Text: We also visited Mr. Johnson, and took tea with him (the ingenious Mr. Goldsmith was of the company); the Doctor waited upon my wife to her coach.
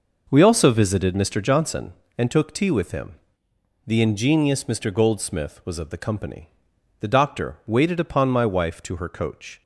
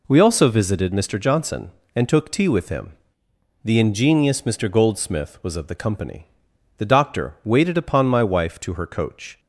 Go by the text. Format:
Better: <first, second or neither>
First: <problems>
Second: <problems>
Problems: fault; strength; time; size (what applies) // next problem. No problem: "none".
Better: second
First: starts louder than the rest; noticeable; until 2.0 s; 5.5 dB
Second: none